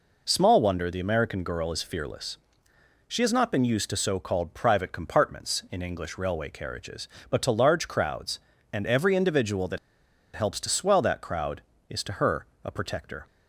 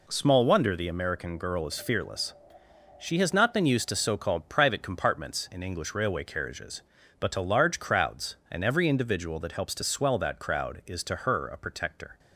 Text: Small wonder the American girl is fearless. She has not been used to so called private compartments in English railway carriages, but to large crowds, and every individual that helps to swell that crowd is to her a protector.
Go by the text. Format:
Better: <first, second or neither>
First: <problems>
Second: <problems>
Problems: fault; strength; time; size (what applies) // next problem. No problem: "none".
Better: second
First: pauses between "that" and "helps"; noticeable; at 9.7 s; 0.57 s long // pauses between "her" and "a"; slight; at 12.4 s; 0.18 s long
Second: none